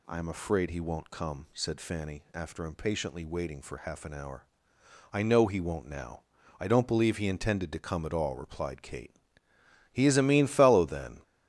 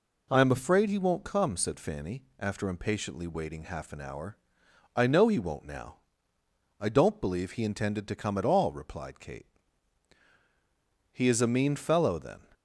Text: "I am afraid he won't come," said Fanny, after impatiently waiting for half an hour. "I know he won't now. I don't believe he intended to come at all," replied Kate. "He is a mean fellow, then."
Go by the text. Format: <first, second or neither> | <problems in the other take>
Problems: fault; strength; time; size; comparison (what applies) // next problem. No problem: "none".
first | skips "for"; at 3.6 s